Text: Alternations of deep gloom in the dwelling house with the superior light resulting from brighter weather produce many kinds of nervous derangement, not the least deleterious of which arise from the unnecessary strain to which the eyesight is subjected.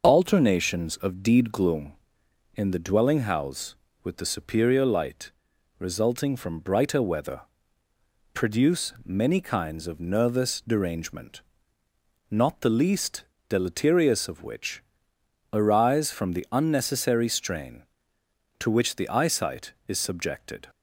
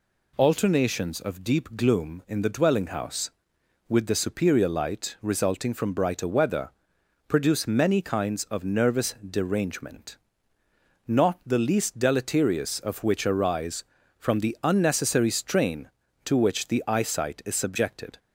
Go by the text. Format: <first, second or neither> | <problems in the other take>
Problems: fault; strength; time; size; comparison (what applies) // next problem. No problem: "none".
second | says "deed" for "deep"; at 1.2 s // pauses between "light" and "resulting"; noticeable; at 5.3 s; 0.48 s long // pauses between "weather" and "produce"; noticeable; at 7.4 s; 0.94 s long; noticeable in the second // pauses between "least" and "deleterious"; slight; at 13.2 s; 0.24 s long // pauses between "which" and "arise"; noticeable; at 14.8 s; 0.72 s long